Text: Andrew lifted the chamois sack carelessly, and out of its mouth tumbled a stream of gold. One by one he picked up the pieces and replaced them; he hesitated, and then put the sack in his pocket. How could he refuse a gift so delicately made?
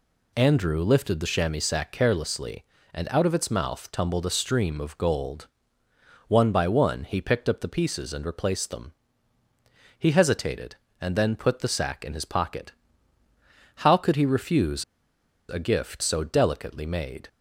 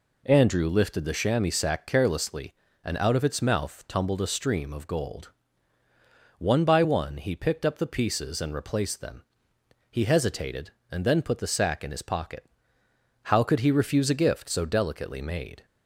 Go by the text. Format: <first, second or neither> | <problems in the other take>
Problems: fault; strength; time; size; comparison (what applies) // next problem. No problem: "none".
second | pauses between "refuse" and "a"; noticeable; at 14.8 s; 0.65 s long